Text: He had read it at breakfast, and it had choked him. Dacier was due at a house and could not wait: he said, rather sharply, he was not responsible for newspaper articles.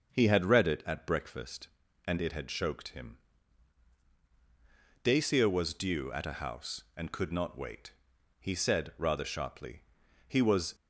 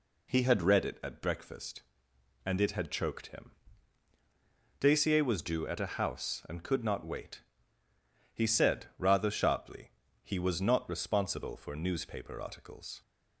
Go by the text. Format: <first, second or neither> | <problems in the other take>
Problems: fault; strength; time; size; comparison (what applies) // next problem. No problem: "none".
second | starts louder than the rest; noticeable; until 1.1 s; 6 dB // stops before "not responsible for newspaper articles"; at 10.7 s